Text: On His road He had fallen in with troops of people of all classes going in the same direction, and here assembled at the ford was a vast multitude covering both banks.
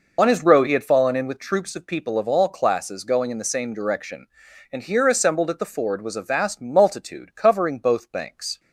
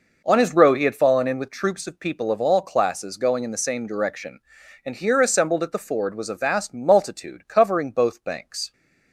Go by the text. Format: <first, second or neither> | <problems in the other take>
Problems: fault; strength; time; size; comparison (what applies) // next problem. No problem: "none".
second | loses the start of "On"; at 0.1 s; 45 ms